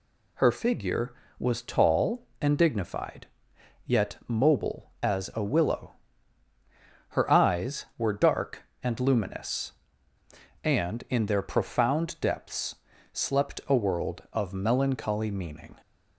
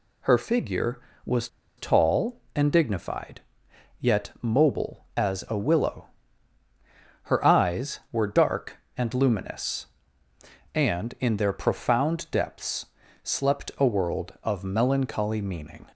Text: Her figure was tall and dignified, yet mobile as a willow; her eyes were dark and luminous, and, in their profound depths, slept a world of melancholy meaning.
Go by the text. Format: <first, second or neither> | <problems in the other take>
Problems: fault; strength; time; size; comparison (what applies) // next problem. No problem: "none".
first | pauses between "was" and "tall"; slight; at 1.4 s; 0.30 s long